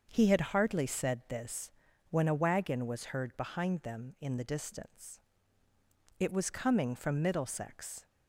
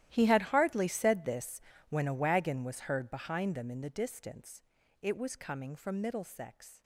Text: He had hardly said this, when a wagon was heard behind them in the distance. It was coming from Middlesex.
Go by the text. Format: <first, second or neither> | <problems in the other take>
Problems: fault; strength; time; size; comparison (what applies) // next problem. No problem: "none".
first | gets quieter; strong; throughout; 17 dB // starts louder than the rest; strong; until 1.1 s; 13 dB; also in the first